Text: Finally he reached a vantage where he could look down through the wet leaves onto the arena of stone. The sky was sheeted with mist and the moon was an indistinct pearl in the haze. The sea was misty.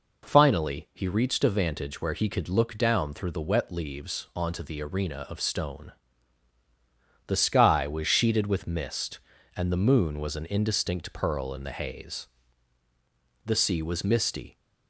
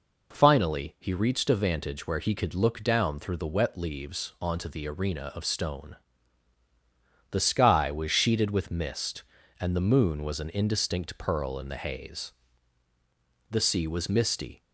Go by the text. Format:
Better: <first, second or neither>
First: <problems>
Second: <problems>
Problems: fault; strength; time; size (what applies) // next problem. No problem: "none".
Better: neither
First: none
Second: none